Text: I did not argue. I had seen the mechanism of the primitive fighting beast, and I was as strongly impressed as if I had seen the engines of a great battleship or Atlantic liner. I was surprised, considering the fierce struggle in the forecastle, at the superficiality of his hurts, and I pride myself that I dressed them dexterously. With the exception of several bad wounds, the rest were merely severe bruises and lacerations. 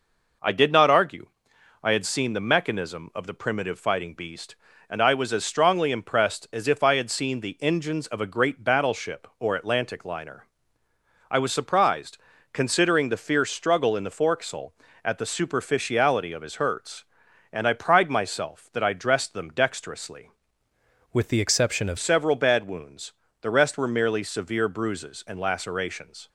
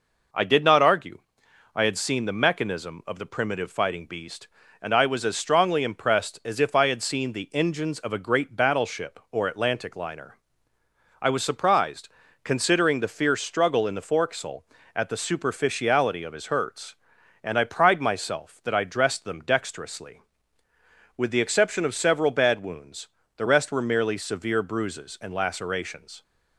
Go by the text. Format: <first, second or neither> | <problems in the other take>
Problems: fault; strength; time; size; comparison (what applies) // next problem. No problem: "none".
second | changes voice from "With" to "of"; from 21.1 to 21.9 s; 0.8 s long